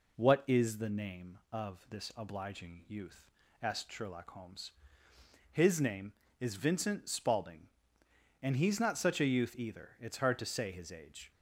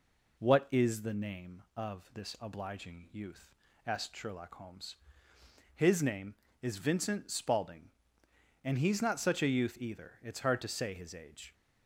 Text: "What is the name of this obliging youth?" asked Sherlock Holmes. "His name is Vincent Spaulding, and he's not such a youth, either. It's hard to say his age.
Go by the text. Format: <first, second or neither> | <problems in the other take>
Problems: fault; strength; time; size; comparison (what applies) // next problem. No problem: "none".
neither | none